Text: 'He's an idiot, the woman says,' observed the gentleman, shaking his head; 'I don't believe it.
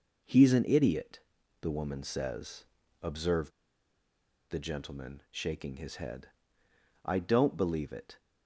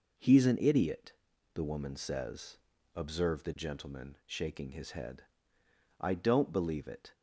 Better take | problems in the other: second | pauses between "observed" and "the"; at 3.5 s; 0.99 s long

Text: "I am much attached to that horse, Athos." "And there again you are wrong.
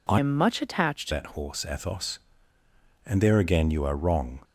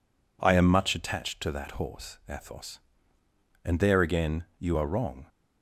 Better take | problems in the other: second | changes voice from "am" to "to"; from 0.1 to 1.1 s; 1.0 s long

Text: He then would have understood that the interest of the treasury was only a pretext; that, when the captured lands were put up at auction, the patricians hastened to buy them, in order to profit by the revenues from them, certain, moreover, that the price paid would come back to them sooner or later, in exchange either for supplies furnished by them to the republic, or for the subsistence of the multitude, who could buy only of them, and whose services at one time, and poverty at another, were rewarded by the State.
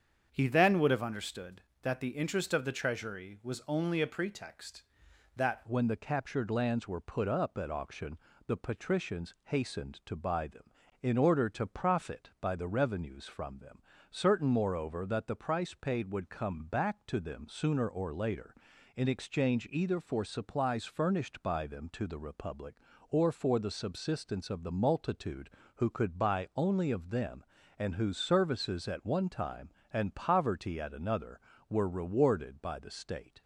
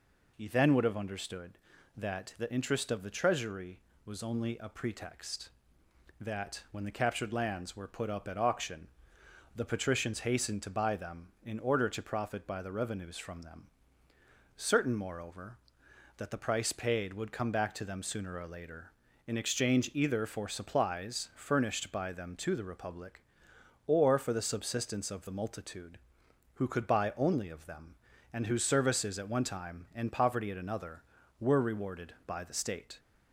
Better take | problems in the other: second | starts louder than the rest; strong; until 1.3 s; 7.5 dB // changes voice at "when"; from 5.6 s on; 27.8 s long

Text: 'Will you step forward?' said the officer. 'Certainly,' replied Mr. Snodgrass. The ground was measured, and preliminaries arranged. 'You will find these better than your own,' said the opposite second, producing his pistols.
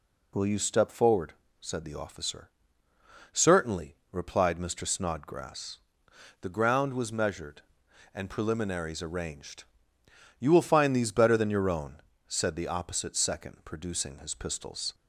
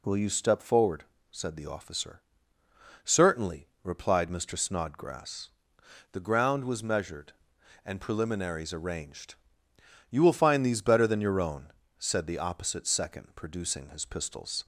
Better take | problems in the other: neither | none

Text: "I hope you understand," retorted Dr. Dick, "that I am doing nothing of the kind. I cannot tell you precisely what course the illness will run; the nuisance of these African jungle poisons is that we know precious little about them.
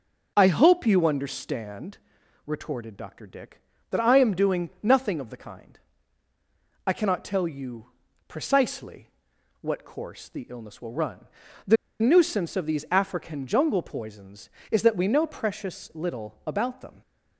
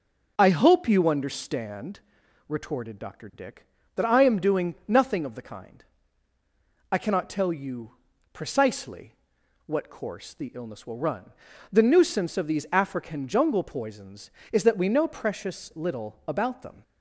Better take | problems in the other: second | pauses between "you" and "precisely"; at 7.8 s; 0.40 s long; also in the second // pauses between "precisely" and "what"; noticeable; at 9.0 s; 0.52 s long; noticeable in the second // pauses between "the" and "nuisance"; slight; at 11.7 s; 0.25 s long

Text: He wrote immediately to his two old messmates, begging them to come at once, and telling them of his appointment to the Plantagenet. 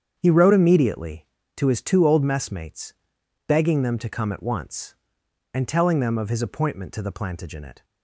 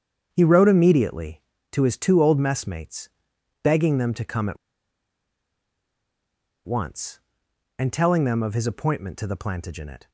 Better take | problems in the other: first | starts louder than the rest; strong; until 1.3 s; 8 dB; strong in the first // pauses between "at" and "once"; strong; at 4.5 s; 2.1 s long

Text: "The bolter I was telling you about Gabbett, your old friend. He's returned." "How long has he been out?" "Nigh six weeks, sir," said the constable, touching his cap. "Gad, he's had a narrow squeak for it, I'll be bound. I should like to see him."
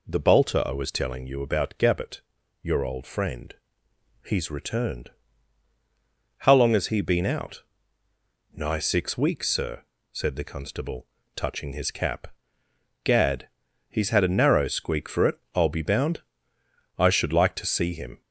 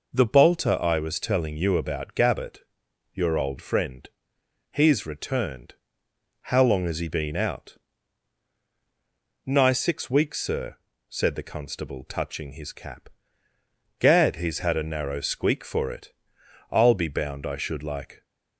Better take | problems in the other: first | stops before "to see him"; at 18.2 s

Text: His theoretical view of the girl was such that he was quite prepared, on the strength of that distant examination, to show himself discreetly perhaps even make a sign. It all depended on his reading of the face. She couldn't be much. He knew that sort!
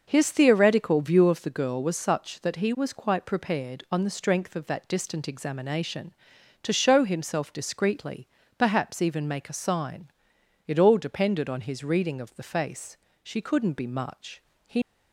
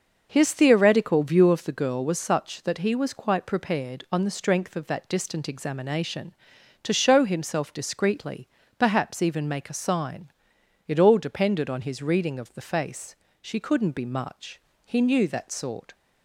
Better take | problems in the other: second | starts louder than the rest; noticeable; until 1.0 s; 6 dB; noticeable in the second // pauses between "discreetly" and "perhaps"; slight; at 8.2 s; 0.32 s long; slight in the second // stops before "knew that sort"; at 14.8 s

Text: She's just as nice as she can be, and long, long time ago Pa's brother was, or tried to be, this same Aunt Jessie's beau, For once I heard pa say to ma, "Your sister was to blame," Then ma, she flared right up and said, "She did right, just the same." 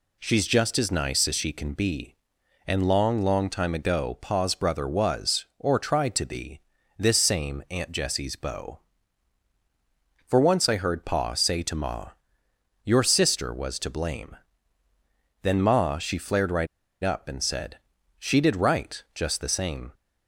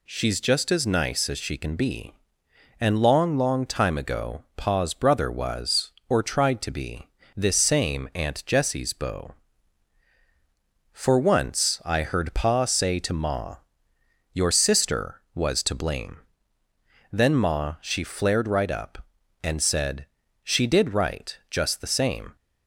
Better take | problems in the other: second | pauses between "right" and "up"; at 16.6 s; 0.36 s long

